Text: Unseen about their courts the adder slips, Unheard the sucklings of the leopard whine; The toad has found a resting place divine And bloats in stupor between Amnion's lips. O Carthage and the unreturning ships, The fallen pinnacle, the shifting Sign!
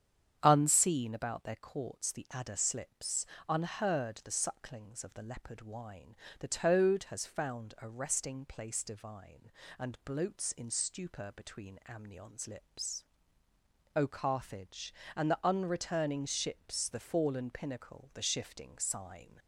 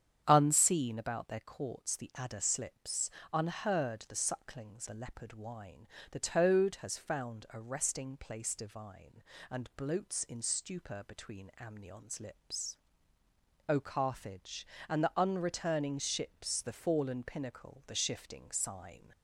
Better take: first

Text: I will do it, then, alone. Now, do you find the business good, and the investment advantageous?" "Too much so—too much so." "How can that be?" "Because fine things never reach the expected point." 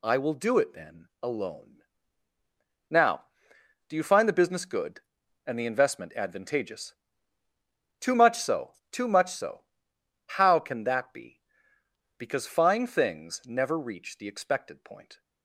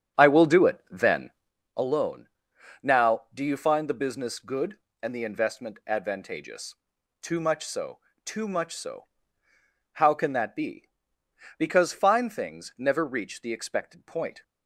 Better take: first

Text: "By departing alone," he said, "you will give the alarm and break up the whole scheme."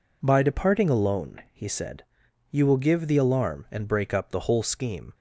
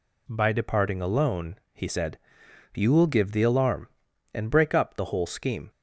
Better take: neither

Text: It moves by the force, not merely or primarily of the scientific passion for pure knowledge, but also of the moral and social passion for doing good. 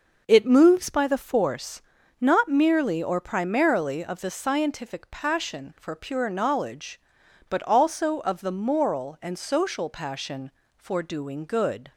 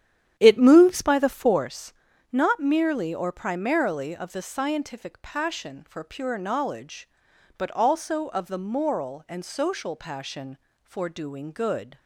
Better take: first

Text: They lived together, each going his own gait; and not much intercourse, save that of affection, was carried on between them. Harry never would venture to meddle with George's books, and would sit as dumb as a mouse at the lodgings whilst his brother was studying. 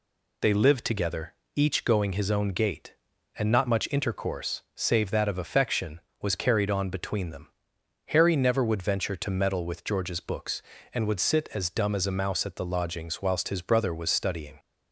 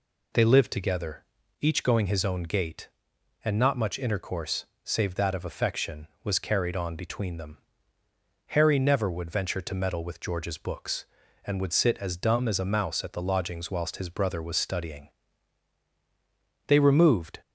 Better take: first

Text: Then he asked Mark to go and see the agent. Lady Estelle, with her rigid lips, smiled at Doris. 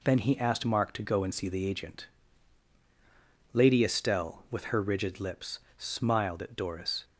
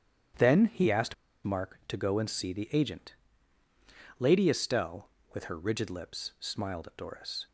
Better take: first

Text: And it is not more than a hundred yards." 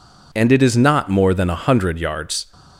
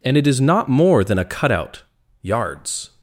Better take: first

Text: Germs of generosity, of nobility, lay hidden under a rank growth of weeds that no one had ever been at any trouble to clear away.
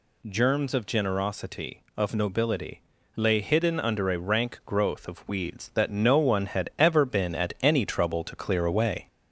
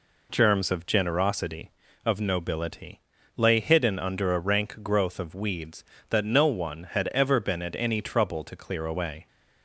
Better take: second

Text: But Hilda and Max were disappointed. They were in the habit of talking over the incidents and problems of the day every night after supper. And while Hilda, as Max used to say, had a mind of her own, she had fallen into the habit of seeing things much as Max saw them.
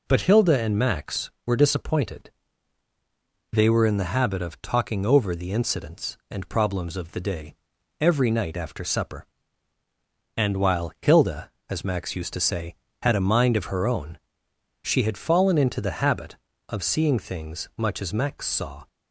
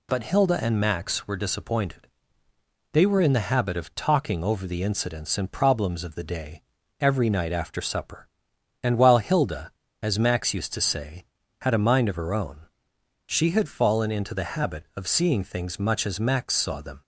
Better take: second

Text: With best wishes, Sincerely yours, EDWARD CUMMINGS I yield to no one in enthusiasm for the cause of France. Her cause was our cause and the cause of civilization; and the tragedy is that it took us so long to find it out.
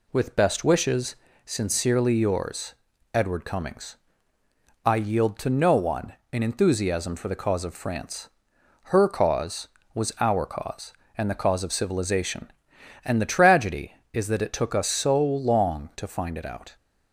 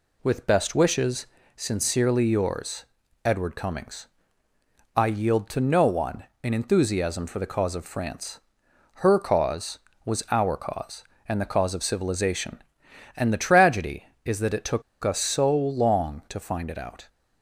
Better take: first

